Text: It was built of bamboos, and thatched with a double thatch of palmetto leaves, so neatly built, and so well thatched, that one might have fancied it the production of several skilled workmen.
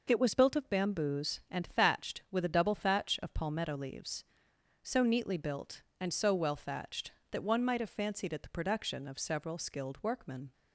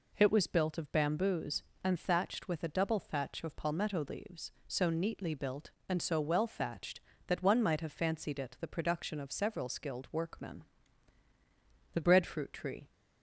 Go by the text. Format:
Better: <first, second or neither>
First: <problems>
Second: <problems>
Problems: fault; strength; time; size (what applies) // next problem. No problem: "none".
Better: first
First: none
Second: goes on to say "The breadfruit tree"; noticeable; from 11.9 s on; 0.98 s long